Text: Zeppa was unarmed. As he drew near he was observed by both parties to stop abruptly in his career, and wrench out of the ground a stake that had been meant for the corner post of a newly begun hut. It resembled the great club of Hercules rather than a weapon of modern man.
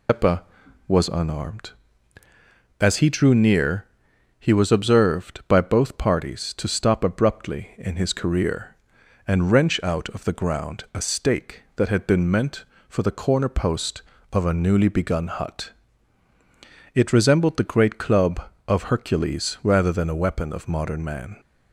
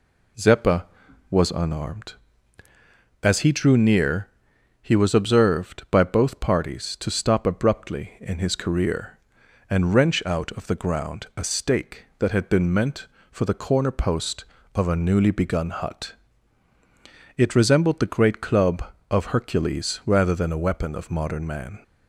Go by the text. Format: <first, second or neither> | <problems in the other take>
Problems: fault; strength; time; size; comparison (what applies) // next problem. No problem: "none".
second | loses the start of "Zeppa"; at 0.0 s; 155 ms // pauses between "near" and "he"; noticeable; at 3.8 s; 0.56 s long; noticeable in the second